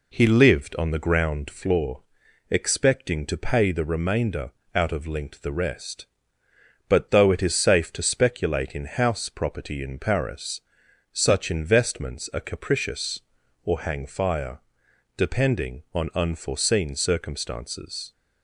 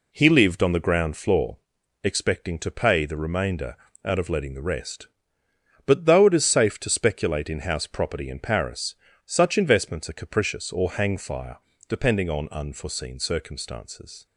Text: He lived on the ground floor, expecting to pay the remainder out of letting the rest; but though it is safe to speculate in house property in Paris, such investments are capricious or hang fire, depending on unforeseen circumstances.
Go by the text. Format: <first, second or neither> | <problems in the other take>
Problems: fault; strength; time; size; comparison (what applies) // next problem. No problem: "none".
second | pauses between "remainder" and "out"; slight; at 4.5 s; 0.24 s long; slight in the second // says "linked" for "letting"; at 5.0 s